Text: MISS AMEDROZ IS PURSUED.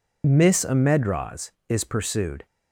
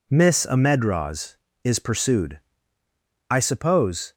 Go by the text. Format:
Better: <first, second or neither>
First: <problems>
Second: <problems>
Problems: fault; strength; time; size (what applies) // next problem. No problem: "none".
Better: first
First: none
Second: goes on to say "I suppose"; noticeable; from 3.2 s on; 0.84 s long